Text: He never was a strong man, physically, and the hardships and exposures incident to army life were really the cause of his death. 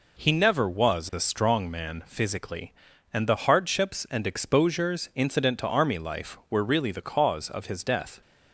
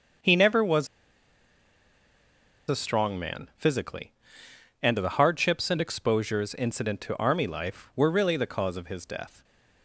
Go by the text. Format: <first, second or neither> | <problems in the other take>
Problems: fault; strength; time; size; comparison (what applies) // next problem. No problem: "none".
first | starts louder than the rest; until 3.0 s; 7 dB // pauses between "was" and "a"; strong; at 0.8 s; 1.8 s long